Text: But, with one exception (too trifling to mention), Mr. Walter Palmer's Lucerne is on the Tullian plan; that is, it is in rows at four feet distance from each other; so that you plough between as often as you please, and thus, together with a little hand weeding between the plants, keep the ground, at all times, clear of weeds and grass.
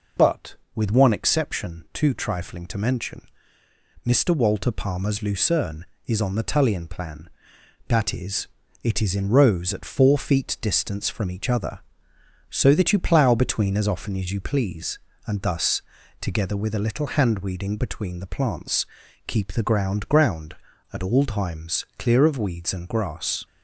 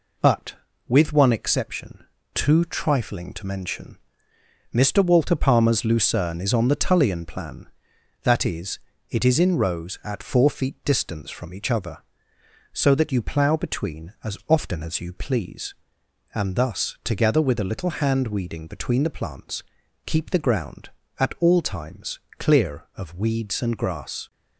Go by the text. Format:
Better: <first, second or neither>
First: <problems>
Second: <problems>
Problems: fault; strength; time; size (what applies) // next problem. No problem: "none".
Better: second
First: says "ground" twice; at 20.0 s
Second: none